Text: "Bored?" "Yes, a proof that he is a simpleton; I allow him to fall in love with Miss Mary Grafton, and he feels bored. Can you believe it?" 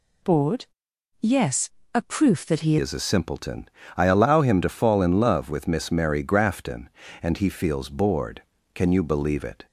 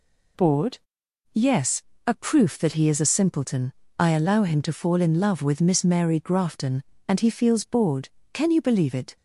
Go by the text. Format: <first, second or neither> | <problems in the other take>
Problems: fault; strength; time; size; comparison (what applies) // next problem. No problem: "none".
second | changes voice at "is"; from 2.8 s on; 6.8 s long